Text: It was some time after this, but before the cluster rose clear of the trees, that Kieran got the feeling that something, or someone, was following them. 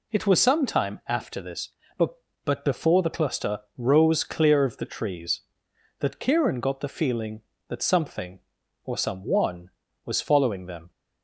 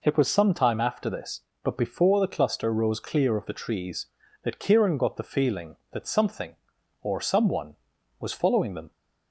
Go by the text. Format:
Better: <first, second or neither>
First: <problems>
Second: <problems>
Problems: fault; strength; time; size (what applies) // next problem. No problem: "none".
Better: second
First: says "but" twice; at 2.4 s // pauses between "cluster" and "rose"; slight; at 3.5 s; 0.18 s long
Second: none